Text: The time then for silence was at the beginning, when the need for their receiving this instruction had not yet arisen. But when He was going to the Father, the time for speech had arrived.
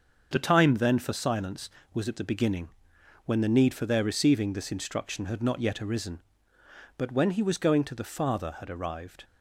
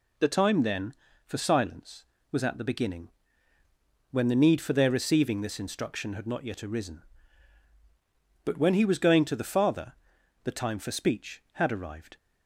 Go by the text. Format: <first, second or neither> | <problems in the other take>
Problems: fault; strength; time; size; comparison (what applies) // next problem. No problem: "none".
second | starts louder than the rest; until 1.3 s; 6.5 dB // skips "the time for speech"; at 8.5 s